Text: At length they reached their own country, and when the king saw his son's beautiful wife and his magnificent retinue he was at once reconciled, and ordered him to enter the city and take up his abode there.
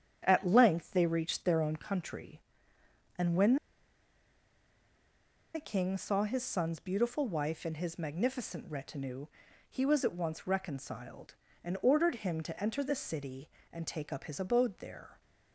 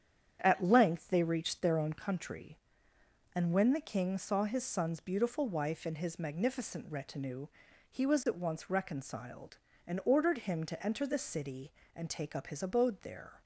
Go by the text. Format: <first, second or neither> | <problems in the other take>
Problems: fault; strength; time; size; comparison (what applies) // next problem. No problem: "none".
second | starts louder than the rest; strong; until 1.2 s; 8.5 dB; strong in the second // pauses between "when" and "the"; strong; at 3.5 s; 1.9 s long // pauses between "retinue" and "he"; at 9.2 s; 0.44 s long; also in the second